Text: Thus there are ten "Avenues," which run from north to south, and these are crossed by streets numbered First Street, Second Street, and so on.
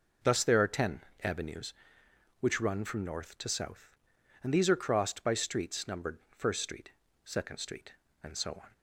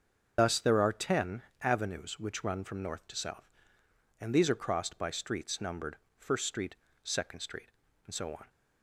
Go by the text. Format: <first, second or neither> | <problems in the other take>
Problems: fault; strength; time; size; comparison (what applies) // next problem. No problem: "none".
first | loses the start of "Thus"; at 0.3 s; 100 ms // starts louder than the rest; until 1.3 s; 6.5 dB // pauses between "ten" and "Avenues"; slight; at 1.4 s; 0.20 s long; slight in the first // pauses between "numbered" and "First"; slight; at 5.9 s; 0.22 s long